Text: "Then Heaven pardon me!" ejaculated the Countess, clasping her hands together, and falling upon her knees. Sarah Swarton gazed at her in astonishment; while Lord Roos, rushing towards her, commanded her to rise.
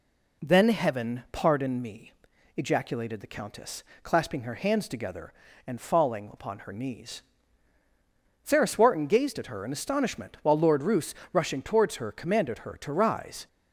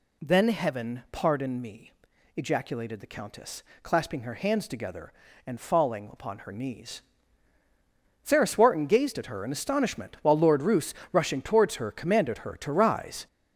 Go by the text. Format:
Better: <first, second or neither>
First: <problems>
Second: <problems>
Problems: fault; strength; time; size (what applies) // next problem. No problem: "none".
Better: first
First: none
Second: gets louder; throughout; 6.5 dB